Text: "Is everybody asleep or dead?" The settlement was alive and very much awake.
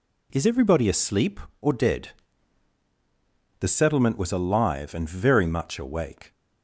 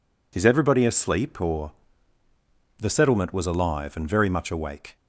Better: first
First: none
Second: skips "dead"; at 2.2 s

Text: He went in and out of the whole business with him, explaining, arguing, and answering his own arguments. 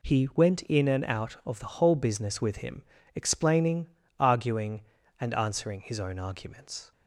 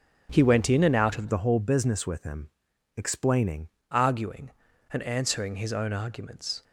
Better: first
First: none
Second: starts louder than the rest; strong; until 1.3 s; 8 dB // changes voice from "the" to "explaining"; from 1.2 to 3.6 s; 2.4 s long

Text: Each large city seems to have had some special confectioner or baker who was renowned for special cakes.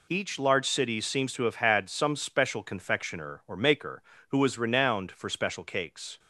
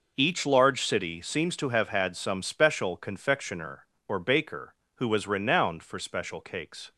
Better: second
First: says "maker" for "baker"; at 3.5 s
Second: none

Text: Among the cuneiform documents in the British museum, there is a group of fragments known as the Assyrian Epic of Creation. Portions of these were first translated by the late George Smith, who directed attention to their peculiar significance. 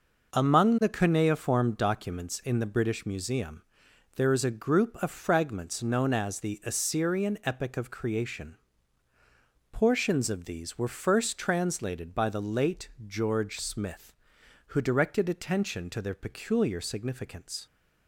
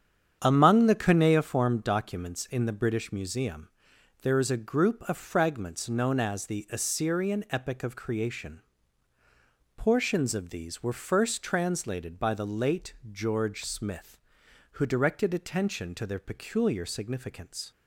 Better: first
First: pauses between "late" and "George"; slight; at 12.8 s; 0.18 s long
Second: starts louder than the rest; strong; until 1.5 s; 8.5 dB // pauses between "late" and "George"; slight; at 12.9 s; 0.18 s long

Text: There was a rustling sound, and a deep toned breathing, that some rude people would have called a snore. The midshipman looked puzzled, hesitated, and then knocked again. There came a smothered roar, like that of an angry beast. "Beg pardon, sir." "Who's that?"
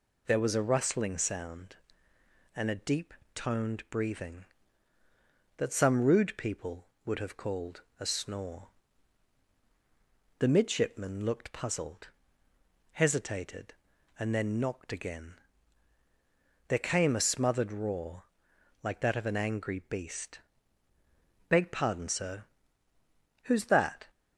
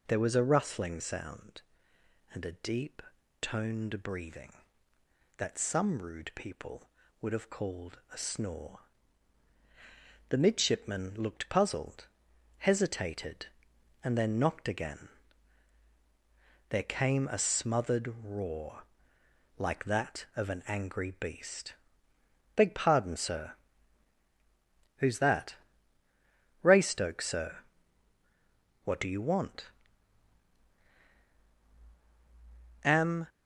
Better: first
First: pauses between "deep" and "toned"; slight; at 3.1 s; 0.22 s long // pauses between "called" and "a"; slight; at 7.8 s; 0.18 s long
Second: pauses between "deep" and "toned"; at 3.0 s; 0.40 s long // pauses between "called" and "a"; slight; at 7.9 s; 0.16 s long // goes on to say "Raystoke sir What do you want Am"; strong; from 26.6 s on; 6.6 s long

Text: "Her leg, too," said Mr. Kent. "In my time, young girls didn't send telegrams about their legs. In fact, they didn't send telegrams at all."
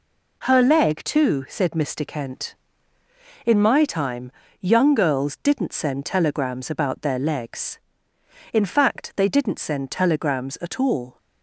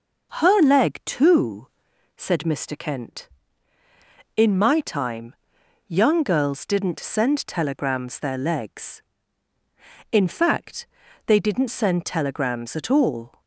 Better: first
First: none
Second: skips "about"; at 8.1 s

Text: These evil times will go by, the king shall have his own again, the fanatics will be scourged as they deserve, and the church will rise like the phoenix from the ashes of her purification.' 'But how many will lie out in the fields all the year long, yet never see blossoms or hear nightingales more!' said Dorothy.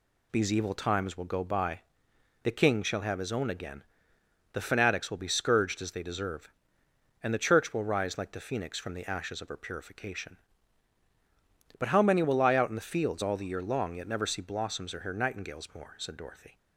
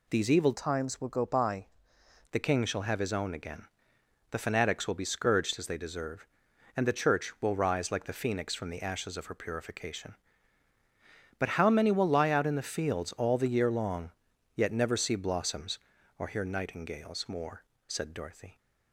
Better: first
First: none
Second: changes voice from "times" to "by"; from 0.5 to 1.6 s; 1.1 s long

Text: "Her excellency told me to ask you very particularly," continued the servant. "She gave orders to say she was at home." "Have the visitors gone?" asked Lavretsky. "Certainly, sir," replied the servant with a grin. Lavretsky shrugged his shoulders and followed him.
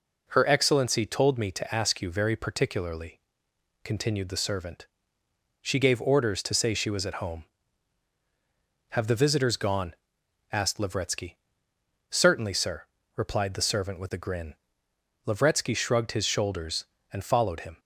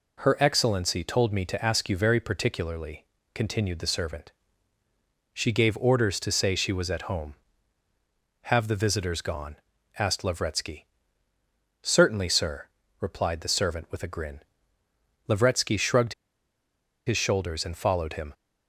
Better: first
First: none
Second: pauses between "shrugged" and "his"; noticeable; at 16.1 s; 0.93 s long

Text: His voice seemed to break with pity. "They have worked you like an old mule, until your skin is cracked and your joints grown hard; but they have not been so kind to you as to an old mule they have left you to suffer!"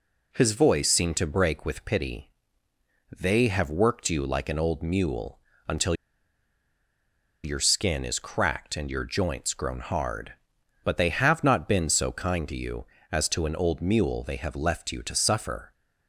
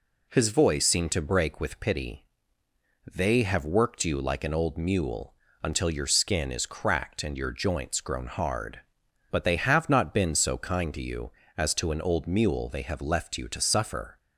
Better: second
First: pauses between "until" and "your"; strong; at 5.9 s; 1.5 s long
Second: none

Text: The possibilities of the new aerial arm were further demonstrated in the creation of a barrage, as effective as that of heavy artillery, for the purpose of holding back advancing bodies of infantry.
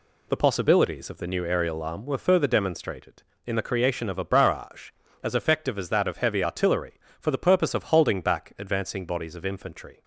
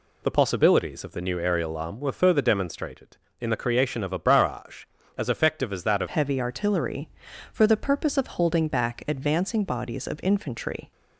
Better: first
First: none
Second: changes voice at "heavy"; from 6.0 s on; 4.9 s long

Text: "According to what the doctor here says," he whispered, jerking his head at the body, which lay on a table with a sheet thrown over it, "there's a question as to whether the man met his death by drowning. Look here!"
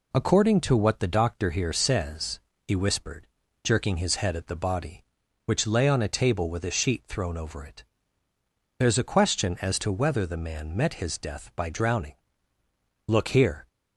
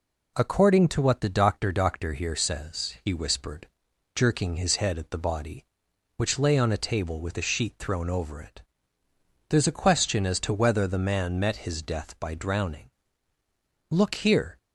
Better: first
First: none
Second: says "doctor" twice; at 1.7 s

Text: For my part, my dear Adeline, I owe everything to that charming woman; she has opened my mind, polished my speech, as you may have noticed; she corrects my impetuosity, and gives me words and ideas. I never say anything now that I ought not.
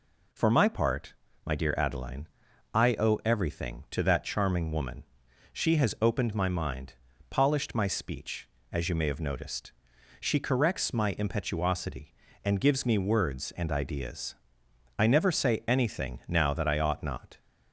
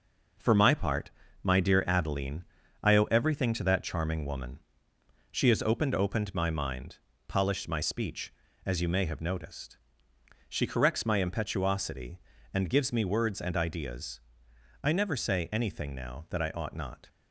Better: first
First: none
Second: says "opened" twice; at 5.9 s

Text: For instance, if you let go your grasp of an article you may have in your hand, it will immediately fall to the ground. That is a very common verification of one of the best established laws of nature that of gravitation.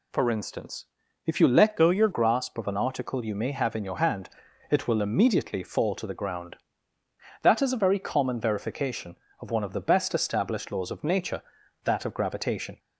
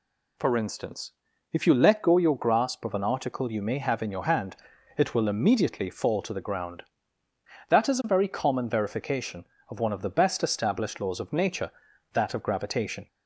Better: second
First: changes voice from "go" to "your"; from 1.7 to 2.0 s; 0.3 s long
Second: none

